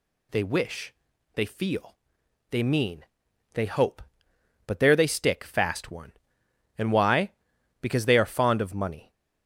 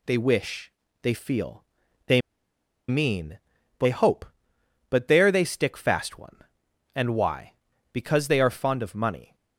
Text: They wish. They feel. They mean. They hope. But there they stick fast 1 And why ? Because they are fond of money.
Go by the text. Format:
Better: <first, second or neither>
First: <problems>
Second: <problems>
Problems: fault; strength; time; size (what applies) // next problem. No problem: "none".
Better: first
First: none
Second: pauses between "They" and "mean"; noticeable; at 2.2 s; 0.68 s long